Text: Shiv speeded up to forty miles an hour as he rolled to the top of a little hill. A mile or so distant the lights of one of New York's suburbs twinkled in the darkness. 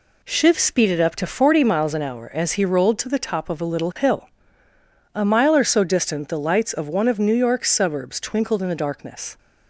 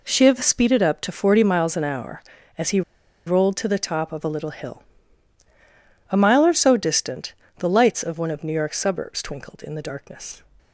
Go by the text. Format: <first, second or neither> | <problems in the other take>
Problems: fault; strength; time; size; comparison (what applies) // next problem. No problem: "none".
first | pauses between "he" and "rolled"; at 2.8 s; 0.45 s long // pauses between "distant" and "the"; slight; at 7.3 s; 0.24 s long